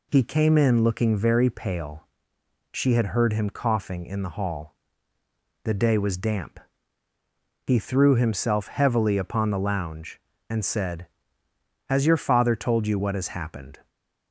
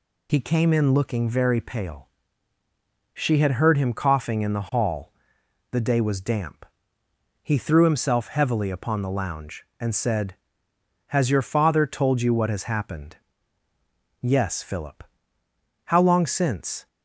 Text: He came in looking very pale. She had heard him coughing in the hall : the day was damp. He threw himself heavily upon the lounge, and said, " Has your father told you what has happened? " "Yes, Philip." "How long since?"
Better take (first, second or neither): second